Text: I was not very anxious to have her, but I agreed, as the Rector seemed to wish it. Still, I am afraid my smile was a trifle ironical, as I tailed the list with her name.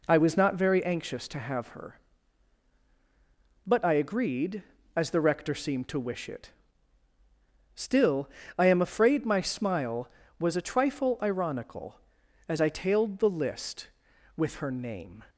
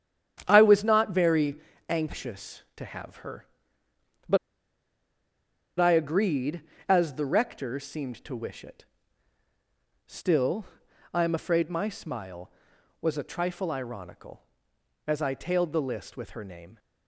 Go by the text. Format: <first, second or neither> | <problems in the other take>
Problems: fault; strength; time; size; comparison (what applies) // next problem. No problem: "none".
first | starts louder than the rest; strong; until 1.4 s; 9.5 dB // pauses between "very" and "anxious"; slight; at 1.5 s; 0.32 s long // pauses between "but" and "I"; strong; at 4.3 s; 1.4 s long